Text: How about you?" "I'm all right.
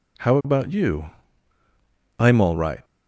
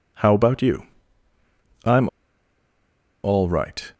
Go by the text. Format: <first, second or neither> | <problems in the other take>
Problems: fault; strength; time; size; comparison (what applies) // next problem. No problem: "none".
first | pauses between "I'm" and "all"; at 2.0 s; 1.1 s long